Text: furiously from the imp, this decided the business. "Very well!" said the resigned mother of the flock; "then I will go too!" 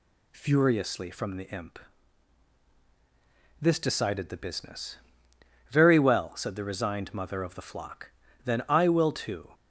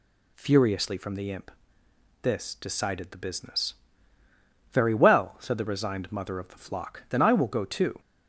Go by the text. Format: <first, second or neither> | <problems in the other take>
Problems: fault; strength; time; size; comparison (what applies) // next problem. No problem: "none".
second | skips "go"; at 9.1 s